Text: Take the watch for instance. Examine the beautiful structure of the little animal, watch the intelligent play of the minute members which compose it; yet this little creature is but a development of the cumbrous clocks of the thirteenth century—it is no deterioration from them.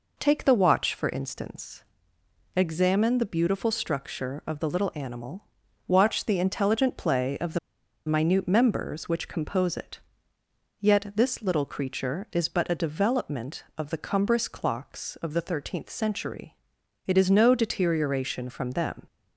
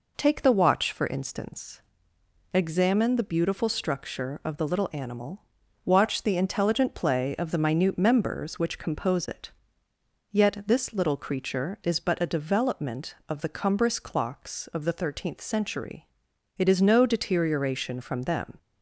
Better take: second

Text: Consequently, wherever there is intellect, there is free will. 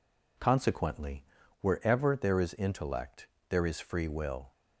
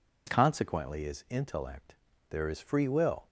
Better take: first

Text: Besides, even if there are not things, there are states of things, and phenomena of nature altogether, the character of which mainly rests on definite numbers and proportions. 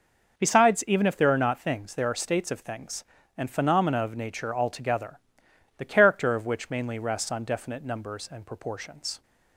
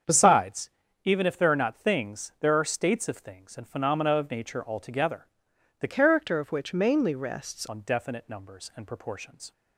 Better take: first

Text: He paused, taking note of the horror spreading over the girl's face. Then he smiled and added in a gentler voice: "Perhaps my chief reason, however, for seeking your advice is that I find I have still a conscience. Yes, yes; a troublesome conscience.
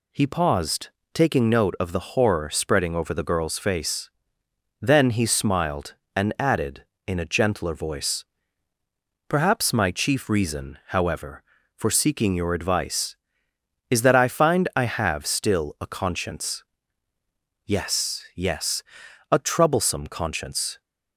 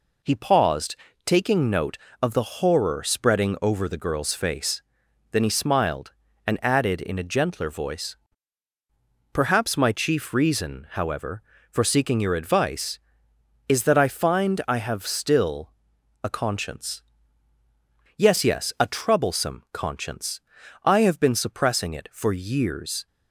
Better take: first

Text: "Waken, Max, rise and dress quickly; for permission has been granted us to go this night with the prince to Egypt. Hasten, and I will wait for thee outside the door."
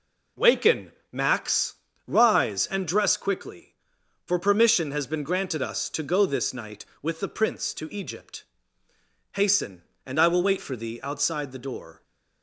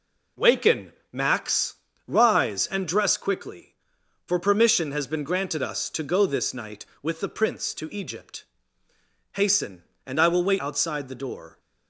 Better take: first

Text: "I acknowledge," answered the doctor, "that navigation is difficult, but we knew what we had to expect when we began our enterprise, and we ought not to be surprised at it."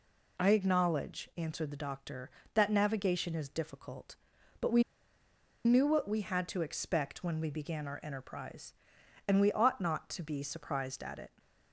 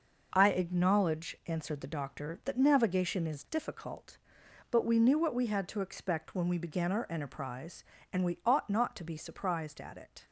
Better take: second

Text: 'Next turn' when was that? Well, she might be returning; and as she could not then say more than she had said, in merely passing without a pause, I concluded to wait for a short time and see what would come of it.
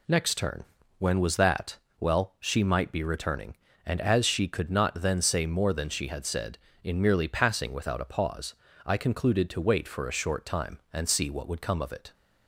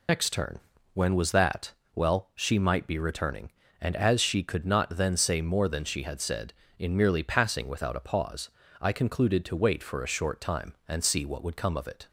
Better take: first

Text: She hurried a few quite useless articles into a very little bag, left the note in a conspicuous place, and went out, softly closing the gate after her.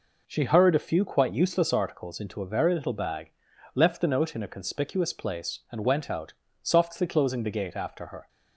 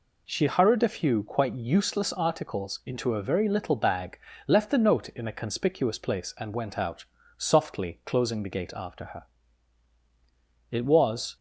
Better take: first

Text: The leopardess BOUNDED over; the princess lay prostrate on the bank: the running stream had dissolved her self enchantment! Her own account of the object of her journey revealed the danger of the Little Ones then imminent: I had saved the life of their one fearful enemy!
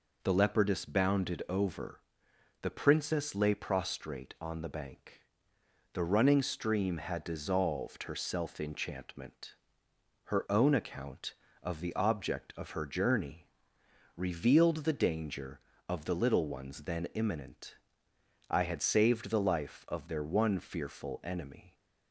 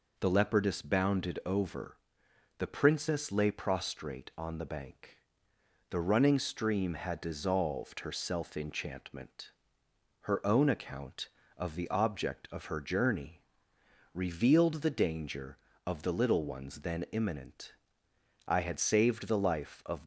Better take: first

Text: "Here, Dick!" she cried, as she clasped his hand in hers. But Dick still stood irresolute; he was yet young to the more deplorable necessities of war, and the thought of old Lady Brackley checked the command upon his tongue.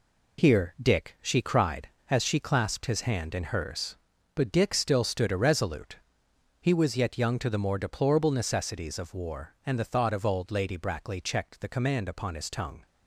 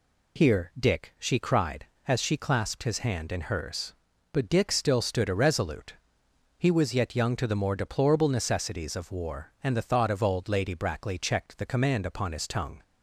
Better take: second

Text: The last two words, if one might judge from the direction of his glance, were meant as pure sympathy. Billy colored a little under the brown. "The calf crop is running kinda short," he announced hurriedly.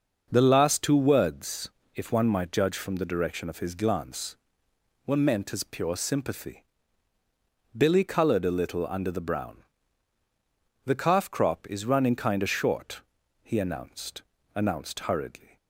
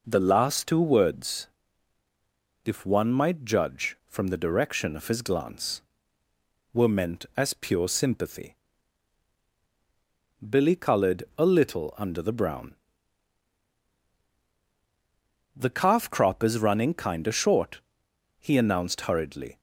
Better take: second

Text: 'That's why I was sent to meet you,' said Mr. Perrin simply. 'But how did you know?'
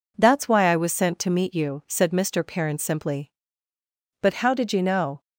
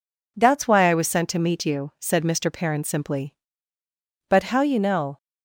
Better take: first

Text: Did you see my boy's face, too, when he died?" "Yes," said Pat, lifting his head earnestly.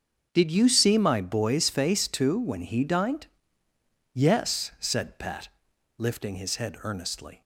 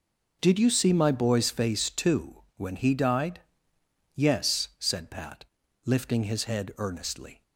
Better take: second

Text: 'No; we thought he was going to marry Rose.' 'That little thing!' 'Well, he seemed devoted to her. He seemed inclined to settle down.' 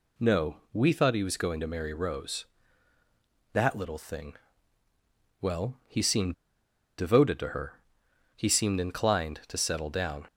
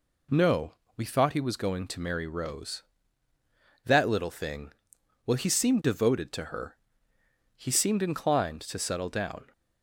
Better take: second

